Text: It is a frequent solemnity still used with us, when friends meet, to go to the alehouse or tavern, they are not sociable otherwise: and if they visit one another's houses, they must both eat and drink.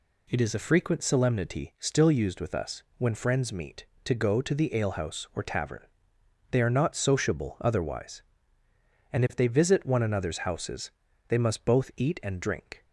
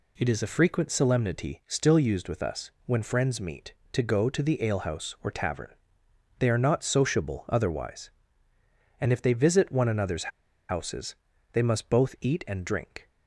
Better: first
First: none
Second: pauses between "another's" and "houses"; at 10.3 s; 0.40 s long

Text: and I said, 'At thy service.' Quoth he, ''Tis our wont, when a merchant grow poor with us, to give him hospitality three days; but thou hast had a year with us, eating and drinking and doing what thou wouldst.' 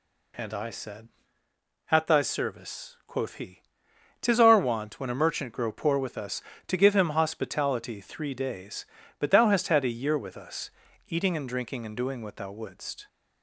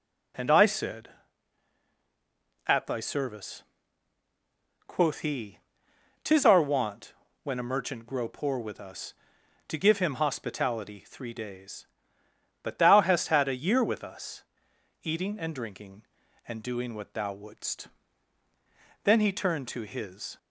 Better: first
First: none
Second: goes on to say "Then he turned to his"; from 19.0 s on; 1.3 s long

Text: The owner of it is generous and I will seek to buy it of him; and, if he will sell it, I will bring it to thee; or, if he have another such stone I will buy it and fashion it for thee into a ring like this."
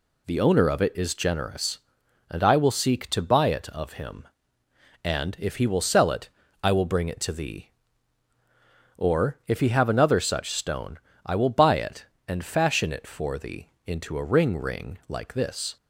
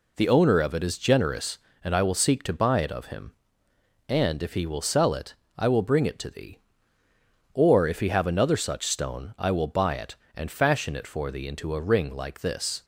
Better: second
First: pauses between "stone" and "I"; slight; at 10.9 s; 0.28 s long // pauses between "thee" and "into"; slight; at 13.6 s; 0.18 s long // says "ring" twice; at 14.5 s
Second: none

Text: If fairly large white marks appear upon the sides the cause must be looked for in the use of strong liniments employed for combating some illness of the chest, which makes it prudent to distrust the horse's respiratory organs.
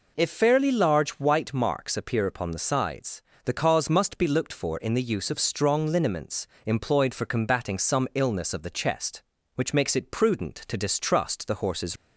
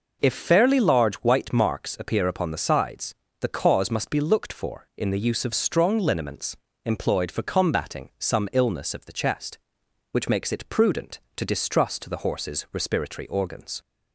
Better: second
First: pauses between "sides" and "the"; slight; at 3.2 s; 0.22 s long // pauses between "liniments" and "employed"; slight; at 6.4 s; 0.20 s long // stops before "respiratory organs"; at 11.9 s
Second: pauses between "sides" and "the"; slight; at 3.1 s; 0.26 s long // pauses between "liniments" and "employed"; slight; at 6.5 s; 0.28 s long

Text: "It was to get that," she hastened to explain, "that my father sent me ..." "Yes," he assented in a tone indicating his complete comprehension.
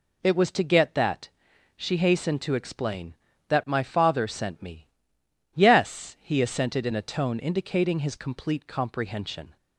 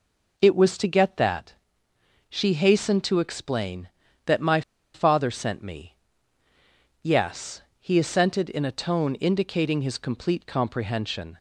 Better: first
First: none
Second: pauses between "my" and "father"; slight; at 4.6 s; 0.33 s long

